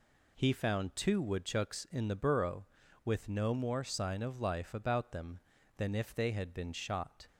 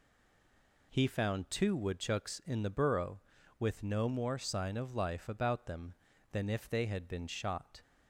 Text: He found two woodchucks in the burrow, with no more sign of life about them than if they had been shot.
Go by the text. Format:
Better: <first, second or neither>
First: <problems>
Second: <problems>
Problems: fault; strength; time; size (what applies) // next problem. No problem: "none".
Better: first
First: none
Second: stays silent before the first word; slight; until 0.9 s; 0.9 s long